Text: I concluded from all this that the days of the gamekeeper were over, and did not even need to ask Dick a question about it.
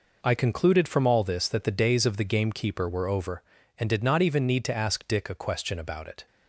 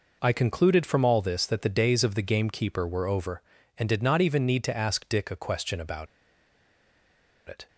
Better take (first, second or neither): first